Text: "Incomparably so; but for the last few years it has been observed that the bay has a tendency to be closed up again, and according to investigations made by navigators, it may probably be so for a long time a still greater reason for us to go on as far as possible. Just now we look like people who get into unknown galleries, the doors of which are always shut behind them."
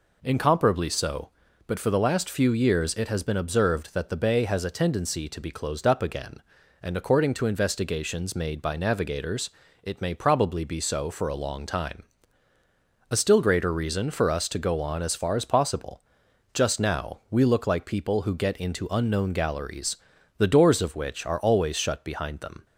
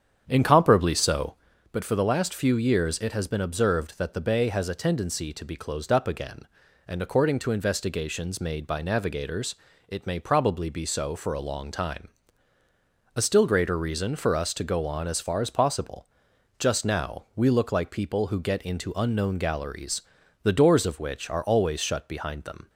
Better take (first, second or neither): first